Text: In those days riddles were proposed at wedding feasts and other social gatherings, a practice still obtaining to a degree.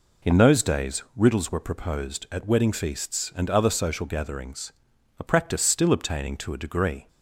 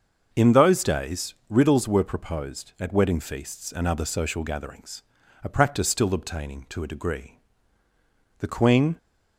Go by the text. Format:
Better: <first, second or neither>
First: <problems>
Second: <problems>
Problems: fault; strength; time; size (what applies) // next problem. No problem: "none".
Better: first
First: none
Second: starts louder than the rest; until 1.3 s; 6.5 dB // pauses between "days" and "riddles"; slight; at 1.3 s; 0.16 s long // goes on to say "The Queen"; from 8.3 s on; 0.58 s long